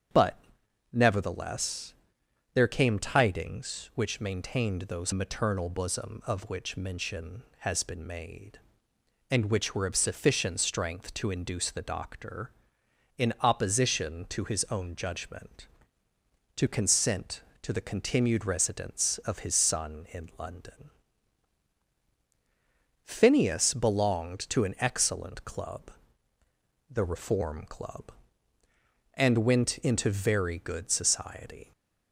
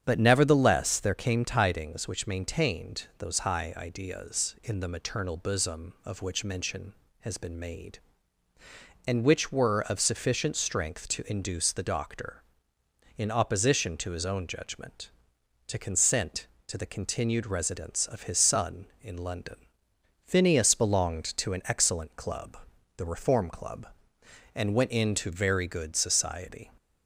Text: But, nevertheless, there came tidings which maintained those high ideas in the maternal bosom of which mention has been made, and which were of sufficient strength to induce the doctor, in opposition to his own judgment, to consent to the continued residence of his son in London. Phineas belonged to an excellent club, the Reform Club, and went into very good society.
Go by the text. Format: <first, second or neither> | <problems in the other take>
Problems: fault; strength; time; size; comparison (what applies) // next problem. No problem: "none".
second | starts louder than the rest; strong; until 1.6 s; 8 dB; strong in the second // skips "high ideas in the"; at 5.1 s